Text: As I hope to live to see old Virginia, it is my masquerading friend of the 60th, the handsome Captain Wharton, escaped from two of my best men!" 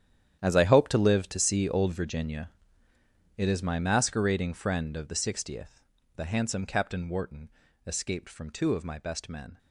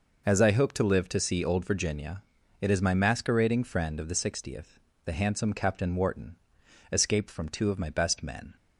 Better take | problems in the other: second | gets quieter; strong; throughout; 15 dB

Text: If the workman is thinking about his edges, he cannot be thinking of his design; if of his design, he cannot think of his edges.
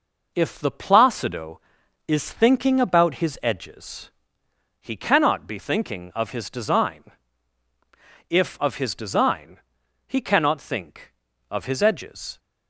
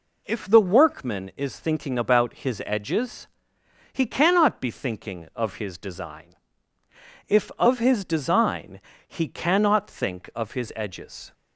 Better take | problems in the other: second | says "placido" for "workman"; at 0.7 s

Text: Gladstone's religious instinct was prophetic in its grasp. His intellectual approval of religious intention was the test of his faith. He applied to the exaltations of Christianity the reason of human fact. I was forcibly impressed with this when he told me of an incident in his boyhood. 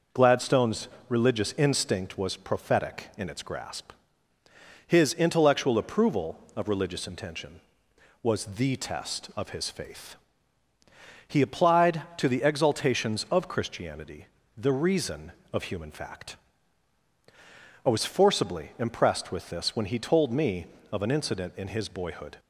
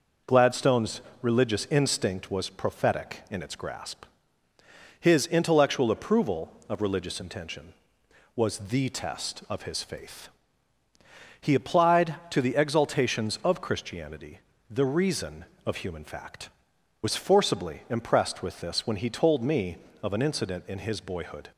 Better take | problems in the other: first | pauses between "Gladstone's" and "religious"; slight; at 1.0 s; 0.20 s long; slight in the first // pauses between "Christianity" and "the"; slight; at 14.3 s; 0.30 s long; slight in the first // skips "I"; at 16.7 s

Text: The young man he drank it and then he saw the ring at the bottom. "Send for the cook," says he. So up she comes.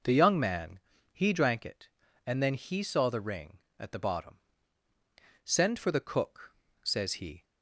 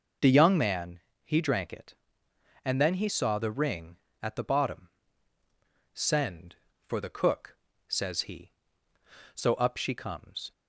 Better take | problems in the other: second | pauses between "man" and "he"; slight; at 0.7 s; 0.32 s long; slight in the second // stops before "So up she comes"; at 7.4 s

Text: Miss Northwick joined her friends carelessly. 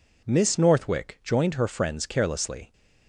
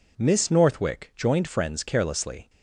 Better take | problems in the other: first | skips "her"; at 1.4 s

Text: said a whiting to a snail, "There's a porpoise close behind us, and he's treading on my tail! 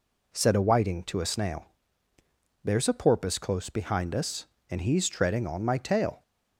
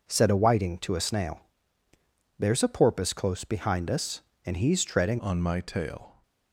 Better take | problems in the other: first | changes voice at "on"; from 5.1 s on; 1.1 s long

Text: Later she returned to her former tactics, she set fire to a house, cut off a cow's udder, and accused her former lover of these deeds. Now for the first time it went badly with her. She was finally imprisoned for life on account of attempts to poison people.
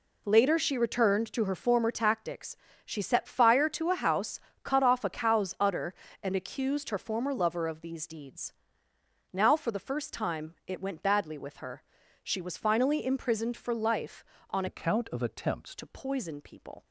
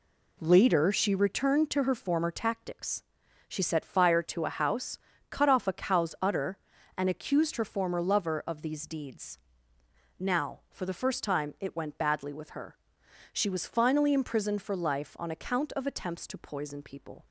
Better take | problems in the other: second | changes voice from "account" to "attempts"; from 14.6 to 15.7 s; 1.1 s long

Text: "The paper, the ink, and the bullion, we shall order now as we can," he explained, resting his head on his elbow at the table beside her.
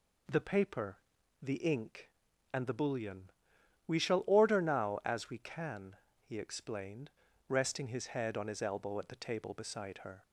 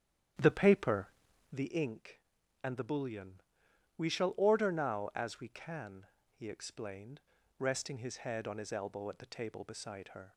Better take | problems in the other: first | starts louder than the rest; strong; until 1.6 s; 10 dB

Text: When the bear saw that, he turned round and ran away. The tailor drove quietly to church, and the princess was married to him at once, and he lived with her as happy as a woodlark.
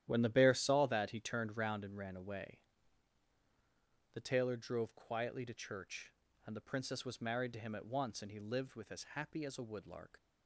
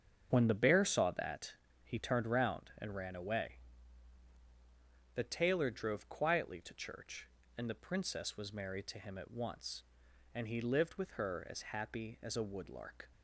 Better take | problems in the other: second | starts louder than the rest; strong; until 1.0 s; 11.5 dB; strong in the second // skips "her"; at 8.9 s

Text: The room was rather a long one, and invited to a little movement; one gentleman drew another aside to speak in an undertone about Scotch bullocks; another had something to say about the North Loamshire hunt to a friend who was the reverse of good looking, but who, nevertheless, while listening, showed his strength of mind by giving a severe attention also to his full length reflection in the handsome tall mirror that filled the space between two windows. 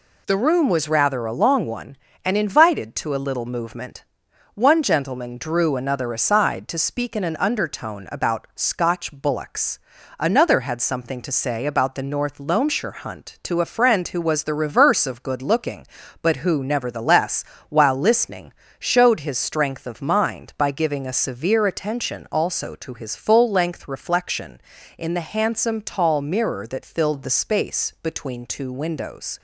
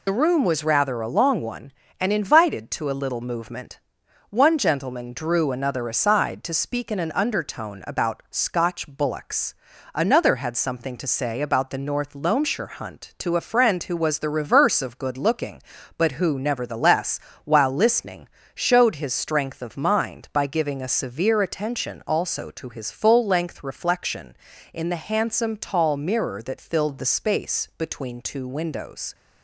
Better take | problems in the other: first | loses the start of "The"; at 0.0 s; 55 ms

